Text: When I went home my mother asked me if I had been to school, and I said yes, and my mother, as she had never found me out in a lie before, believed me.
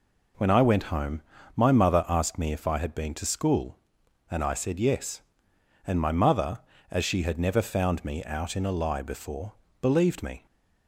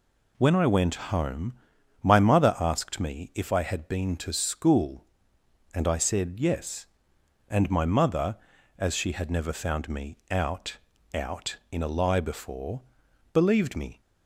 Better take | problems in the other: first | pauses between "home" and "my"; noticeable; at 1.5 s; 0.50 s long; slight in the first // says "out" twice; at 11.1 s

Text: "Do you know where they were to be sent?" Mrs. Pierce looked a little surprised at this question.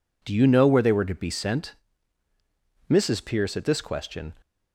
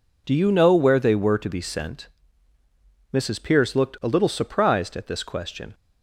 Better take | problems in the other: second | skips "looked a little surprised"; at 3.5 s

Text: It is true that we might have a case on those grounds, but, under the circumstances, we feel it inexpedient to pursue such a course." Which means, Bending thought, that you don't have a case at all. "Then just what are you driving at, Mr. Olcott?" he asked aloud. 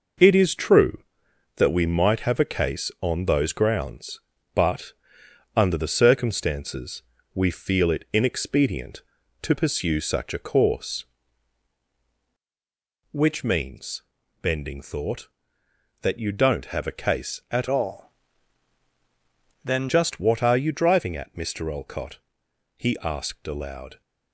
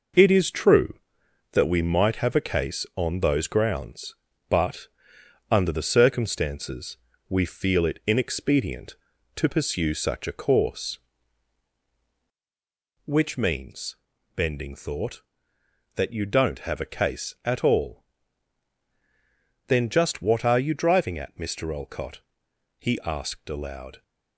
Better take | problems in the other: second | changes voice from "all" to "Then"; from 17.7 to 19.8 s; 2.1 s long

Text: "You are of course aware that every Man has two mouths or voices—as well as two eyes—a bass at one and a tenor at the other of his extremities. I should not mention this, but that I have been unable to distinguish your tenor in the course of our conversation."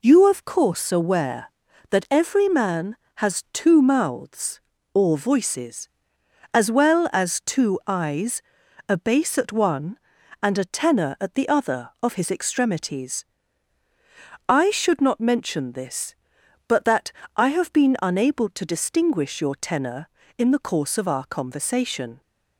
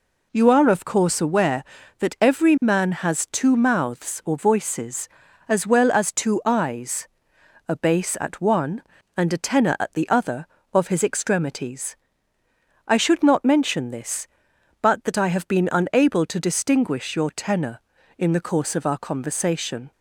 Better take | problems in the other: second | skips "are"; at 0.2 s // pauses between "that" and "I"; slight; at 17.1 s; 0.24 s long

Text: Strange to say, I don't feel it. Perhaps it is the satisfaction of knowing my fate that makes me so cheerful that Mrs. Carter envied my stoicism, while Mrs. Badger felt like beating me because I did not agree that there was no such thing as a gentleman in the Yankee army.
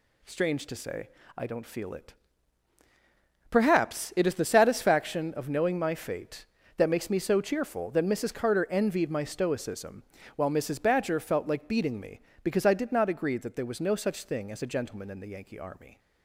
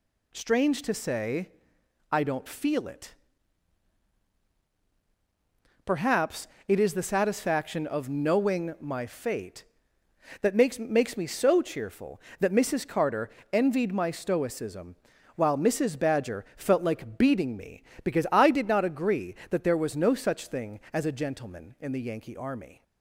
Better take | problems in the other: first | pauses between "Perhaps" and "it"; slight; at 6.4 s; 0.20 s long // says "makes" twice; at 10.7 s // pauses between "Carter" and "envied"; slight; at 13.3 s; 0.20 s long

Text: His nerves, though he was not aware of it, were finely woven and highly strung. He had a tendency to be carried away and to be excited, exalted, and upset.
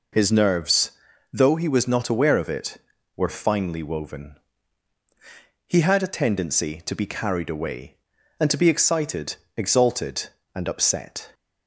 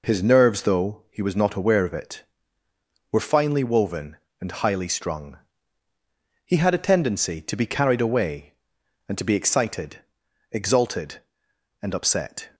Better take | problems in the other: second | skips "and highly strung"; at 5.0 s

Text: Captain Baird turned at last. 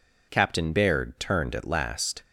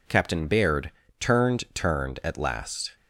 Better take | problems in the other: first | pauses between "Baird" and "turned"; slight; at 0.9 s; 0.28 s long // says "turned" twice; at 1.7 s

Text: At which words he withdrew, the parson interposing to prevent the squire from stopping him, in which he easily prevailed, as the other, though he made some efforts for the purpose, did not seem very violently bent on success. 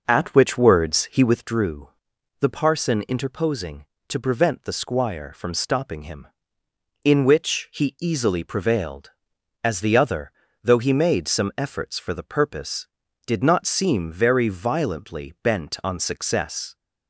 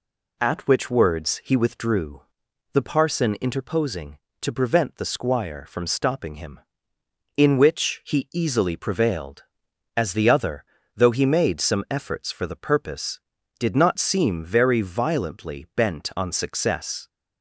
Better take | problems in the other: second | starts louder than the rest; noticeable; until 1.5 s; 5.5 dB

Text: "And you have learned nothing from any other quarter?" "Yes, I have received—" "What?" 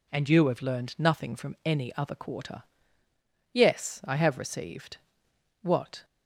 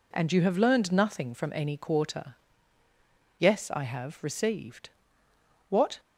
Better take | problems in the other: first | skips "other"; at 1.7 s

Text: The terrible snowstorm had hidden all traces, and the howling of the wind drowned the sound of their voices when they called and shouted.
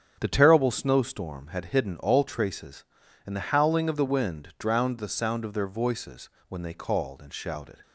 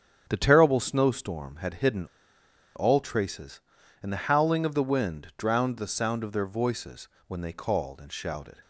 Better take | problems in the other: first | starts louder than the rest; strong; until 1.3 s; 8.5 dB; strong in the first // pauses between "hidden" and "all"; noticeable; at 2.0 s; 0.71 s long // pauses between "voices" and "when"; slight; at 7.0 s; 0.18 s long; slight in the first

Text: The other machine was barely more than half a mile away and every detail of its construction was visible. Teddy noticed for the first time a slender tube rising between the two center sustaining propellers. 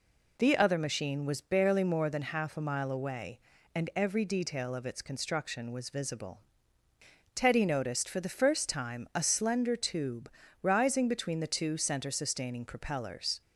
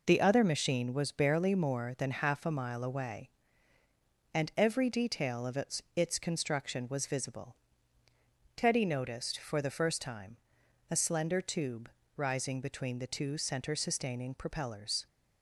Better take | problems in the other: first | says "its" twice; at 5.9 s // pauses between "time" and "a"; noticeable; at 10.3 s; 0.54 s long // pauses between "tube" and "rising"; slight; at 11.8 s; 0.28 s long; slight in the first

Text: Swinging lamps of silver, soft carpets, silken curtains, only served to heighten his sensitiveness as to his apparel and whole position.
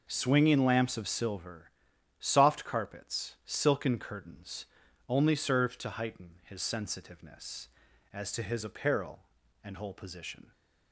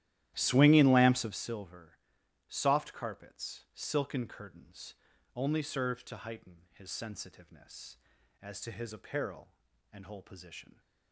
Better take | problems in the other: first | starts louder than the rest; strong; until 1.4 s; 13 dB

